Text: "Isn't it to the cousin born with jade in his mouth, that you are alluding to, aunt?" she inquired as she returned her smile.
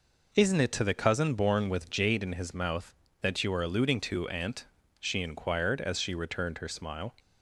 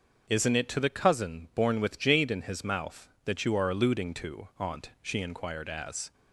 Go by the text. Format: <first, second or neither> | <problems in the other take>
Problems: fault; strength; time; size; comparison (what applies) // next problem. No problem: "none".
first | starts louder than the rest; until 1.2 s; 6.5 dB // stops before "she returned her smile"; at 6.1 s